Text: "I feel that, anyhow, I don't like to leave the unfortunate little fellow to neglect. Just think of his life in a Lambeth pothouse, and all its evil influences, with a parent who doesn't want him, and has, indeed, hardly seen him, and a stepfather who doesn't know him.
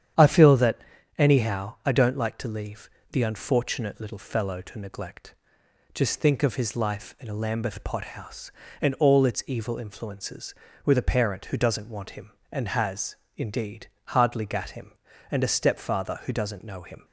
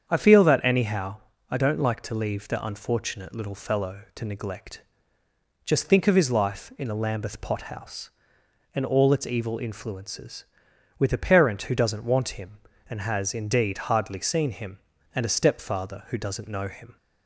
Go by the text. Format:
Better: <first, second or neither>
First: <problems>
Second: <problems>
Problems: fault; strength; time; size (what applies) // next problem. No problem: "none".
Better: second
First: starts louder than the rest; strong; until 1.5 s; 9 dB // pauses between "leave" and "the"; slight; at 2.8 s; 0.22 s long // says "gat" for "seen"; at 14.4 s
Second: starts louder than the rest; strong; until 1.0 s; 7.5 dB